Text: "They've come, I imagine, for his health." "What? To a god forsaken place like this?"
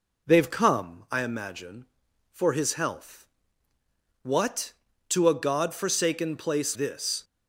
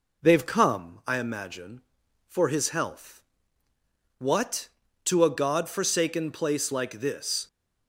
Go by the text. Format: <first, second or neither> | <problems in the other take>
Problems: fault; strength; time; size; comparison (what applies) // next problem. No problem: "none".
second | skips "like"; at 6.7 s